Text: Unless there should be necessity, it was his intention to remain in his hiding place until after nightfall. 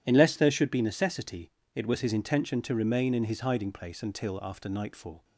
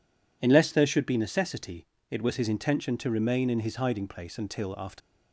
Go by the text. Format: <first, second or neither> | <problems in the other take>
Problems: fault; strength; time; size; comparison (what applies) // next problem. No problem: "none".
first | stops before "nightfall"; at 5.0 s